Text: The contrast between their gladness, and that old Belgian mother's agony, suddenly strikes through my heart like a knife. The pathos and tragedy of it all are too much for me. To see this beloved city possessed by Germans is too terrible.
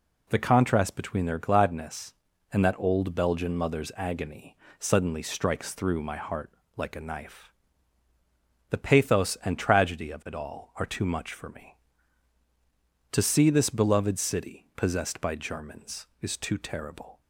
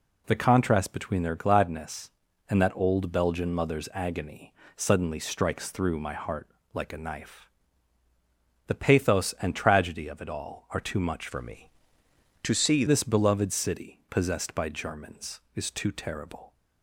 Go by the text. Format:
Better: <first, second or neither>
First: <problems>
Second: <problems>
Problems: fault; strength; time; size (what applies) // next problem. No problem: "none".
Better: first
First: pauses between "heart" and "like"; slight; at 6.5 s; 0.24 s long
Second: pauses between "heart" and "like"; slight; at 6.4 s; 0.24 s long // changes voice from "for" to "see"; from 11.2 to 12.8 s; 1.6 s long